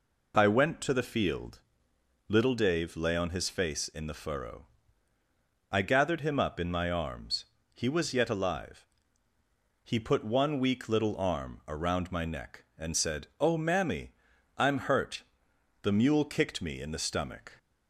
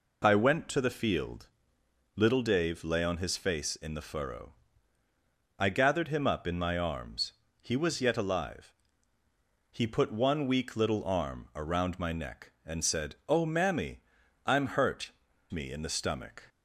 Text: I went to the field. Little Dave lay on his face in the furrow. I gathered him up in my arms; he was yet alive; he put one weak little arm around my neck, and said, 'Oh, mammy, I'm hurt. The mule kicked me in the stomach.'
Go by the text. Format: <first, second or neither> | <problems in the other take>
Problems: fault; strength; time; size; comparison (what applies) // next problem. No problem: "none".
first | skips "The mule kicked"; at 15.3 s